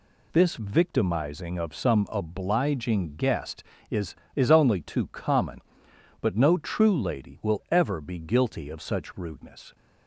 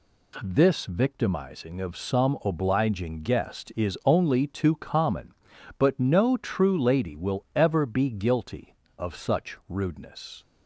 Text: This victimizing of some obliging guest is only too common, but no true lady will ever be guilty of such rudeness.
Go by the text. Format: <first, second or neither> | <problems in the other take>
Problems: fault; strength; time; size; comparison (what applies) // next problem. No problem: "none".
second | says "is" twice; at 4.3 s